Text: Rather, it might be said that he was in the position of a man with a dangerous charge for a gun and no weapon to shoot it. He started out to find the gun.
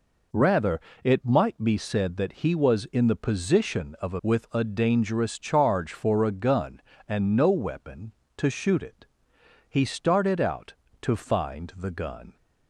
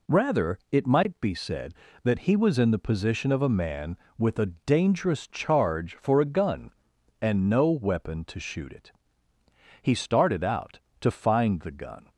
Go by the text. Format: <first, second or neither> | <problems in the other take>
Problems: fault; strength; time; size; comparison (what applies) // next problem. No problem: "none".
second | skips "man"; at 4.2 s